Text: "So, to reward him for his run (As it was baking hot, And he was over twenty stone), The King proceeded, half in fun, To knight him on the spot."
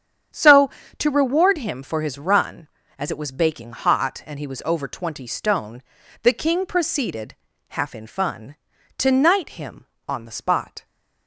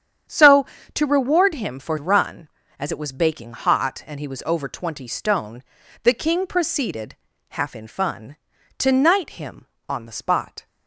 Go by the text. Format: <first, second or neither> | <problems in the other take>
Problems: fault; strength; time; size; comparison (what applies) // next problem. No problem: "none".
first | starts louder than the rest; strong; until 1.5 s; 9 dB; strong in the first // skips "his"; at 1.9 s